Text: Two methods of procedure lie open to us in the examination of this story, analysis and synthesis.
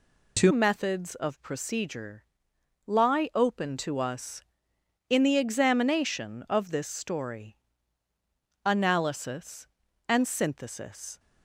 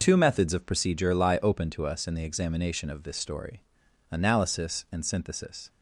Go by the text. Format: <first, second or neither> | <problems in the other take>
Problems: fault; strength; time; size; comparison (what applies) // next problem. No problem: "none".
second | changes voice at "methods"; from 0.4 s on; 10.7 s long // pauses between "procedure" and "lie"; noticeable; at 2.2 s; 0.64 s long